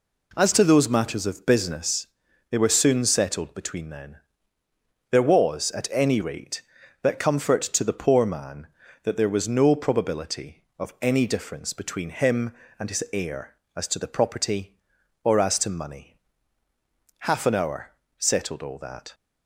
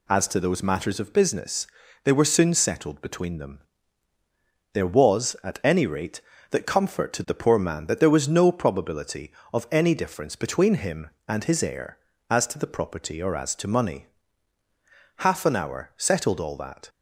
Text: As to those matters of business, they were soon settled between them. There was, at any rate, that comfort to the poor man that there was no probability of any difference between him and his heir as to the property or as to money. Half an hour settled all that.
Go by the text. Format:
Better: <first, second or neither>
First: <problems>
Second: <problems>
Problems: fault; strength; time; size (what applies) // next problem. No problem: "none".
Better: second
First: says "then" for "them"; at 3.9 s // pauses between "hour" and "settled"; slight; at 17.9 s; 0.28 s long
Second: none